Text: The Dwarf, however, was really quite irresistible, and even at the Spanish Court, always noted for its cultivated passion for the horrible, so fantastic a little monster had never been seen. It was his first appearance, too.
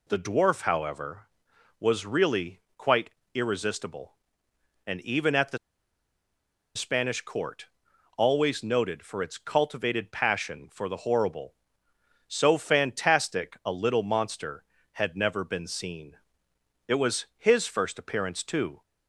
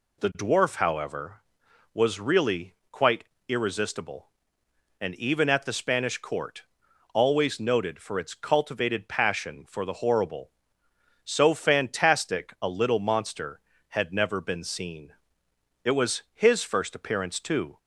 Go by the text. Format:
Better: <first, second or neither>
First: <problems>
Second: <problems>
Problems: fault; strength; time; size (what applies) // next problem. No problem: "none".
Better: second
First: pauses between "really" and "quite"; slight; at 2.5 s; 0.18 s long // pauses between "quite" and "irresistible"; slight; at 3.0 s; 0.24 s long // pauses between "the" and "Spanish"; at 5.5 s; 1.1 s long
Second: pauses between "really" and "quite"; slight; at 2.7 s; 0.18 s long // pauses between "quite" and "irresistible"; slight; at 3.2 s; 0.24 s long